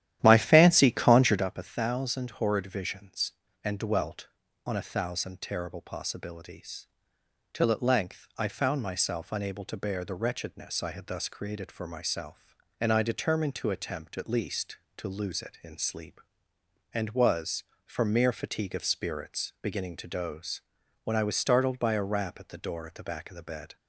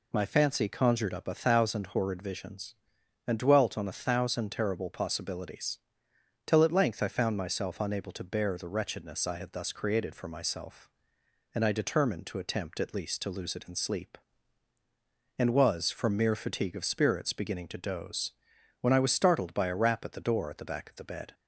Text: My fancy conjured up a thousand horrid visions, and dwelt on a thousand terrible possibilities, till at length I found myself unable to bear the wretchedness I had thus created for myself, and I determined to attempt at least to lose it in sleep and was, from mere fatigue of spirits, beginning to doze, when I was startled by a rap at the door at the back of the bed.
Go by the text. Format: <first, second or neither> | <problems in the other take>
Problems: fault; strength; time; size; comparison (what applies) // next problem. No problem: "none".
second | starts louder than the rest; strong; until 1.4 s; 12 dB